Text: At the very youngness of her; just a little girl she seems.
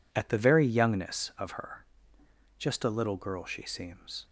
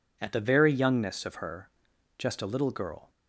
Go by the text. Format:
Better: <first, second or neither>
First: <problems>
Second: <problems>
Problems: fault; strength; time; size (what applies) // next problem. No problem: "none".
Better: first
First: none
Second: stops before "she seems"; at 3.0 s